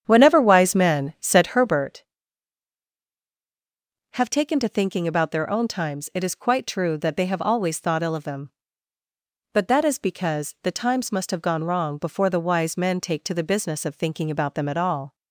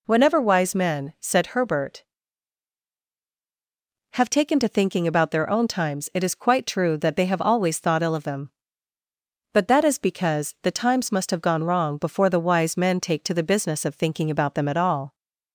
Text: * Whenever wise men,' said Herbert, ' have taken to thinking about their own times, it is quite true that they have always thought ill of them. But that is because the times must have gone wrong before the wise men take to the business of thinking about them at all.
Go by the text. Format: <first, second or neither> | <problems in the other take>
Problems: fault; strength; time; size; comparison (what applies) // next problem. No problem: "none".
second | starts louder than the rest; strong; until 2.0 s; 8.5 dB